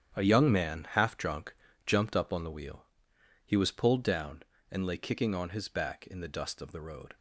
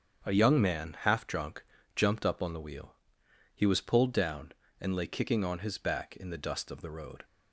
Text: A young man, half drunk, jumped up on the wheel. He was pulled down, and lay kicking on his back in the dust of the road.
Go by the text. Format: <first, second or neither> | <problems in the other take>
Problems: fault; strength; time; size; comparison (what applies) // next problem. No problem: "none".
second | gets quieter; strong; throughout; 11 dB // starts louder than the rest; strong; until 1.2 s; 9.5 dB; strong in the second